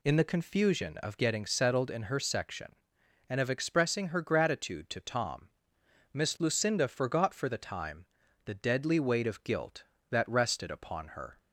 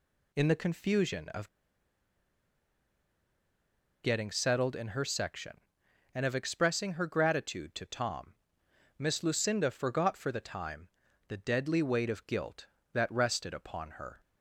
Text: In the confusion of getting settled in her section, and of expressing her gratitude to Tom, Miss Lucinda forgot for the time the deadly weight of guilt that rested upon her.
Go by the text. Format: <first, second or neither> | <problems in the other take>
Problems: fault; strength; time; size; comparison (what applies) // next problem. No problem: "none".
first | pauses between "of" and "getting"; strong; at 1.4 s; 2.5 s long // pauses between "time" and "the"; at 10.8 s; 0.40 s long; also in the first